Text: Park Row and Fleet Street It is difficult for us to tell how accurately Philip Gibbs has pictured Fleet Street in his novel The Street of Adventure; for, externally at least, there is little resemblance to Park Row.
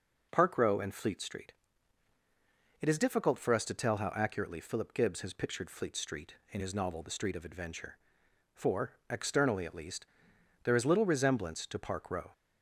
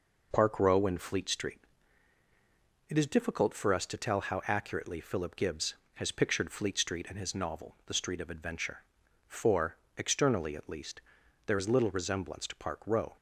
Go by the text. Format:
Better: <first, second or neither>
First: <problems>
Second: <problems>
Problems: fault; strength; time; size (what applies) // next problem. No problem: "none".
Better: neither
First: pauses between "Street" and "It"; strong; at 1.5 s; 1.2 s long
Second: pauses between "Street" and "It"; strong; at 1.6 s; 1.2 s long